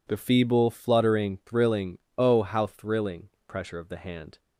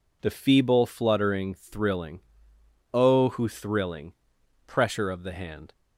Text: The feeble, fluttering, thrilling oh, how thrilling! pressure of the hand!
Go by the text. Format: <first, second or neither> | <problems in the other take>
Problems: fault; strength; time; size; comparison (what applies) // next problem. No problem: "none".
first | pauses between "thrilling" and "oh"; noticeable; at 2.2 s; 0.70 s long; slight in the first // says "who" for "how"; at 3.2 s